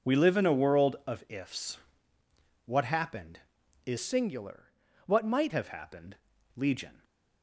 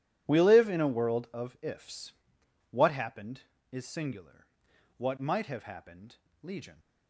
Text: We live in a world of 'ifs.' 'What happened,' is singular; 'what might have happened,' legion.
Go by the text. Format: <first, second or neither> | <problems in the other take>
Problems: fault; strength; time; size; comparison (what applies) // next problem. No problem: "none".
second | changes voice from "singular" to "might"; from 3.9 to 5.5 s; 1.6 s long